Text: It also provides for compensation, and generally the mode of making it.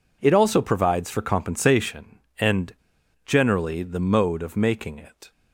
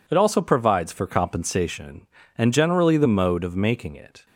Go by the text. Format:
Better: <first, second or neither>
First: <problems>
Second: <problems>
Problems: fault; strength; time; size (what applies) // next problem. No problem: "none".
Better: second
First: pauses between "and" and "generally"; noticeable; at 2.7 s; 0.50 s long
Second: none